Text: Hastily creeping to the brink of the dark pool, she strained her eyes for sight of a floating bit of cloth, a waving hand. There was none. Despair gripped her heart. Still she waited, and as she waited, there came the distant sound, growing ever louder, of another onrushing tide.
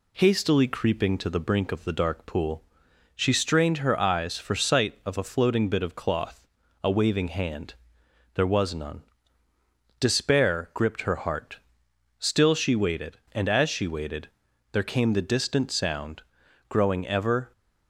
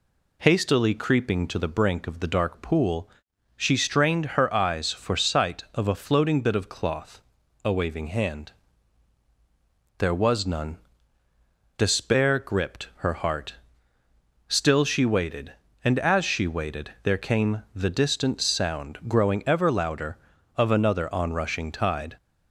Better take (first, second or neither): second